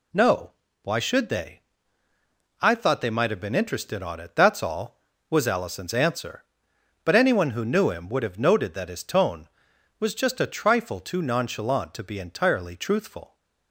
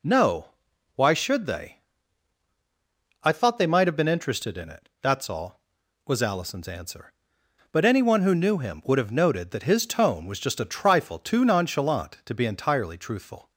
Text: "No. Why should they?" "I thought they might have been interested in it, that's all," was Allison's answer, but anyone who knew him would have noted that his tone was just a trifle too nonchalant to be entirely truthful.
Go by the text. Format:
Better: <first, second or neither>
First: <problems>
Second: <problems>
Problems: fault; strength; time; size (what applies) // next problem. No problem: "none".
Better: second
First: says "on" for "in"; at 4.0 s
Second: none